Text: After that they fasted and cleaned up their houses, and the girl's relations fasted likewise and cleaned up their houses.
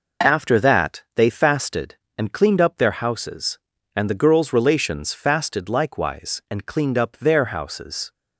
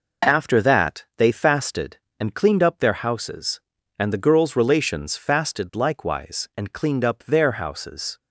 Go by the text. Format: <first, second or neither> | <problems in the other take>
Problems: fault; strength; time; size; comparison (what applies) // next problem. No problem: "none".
neither | none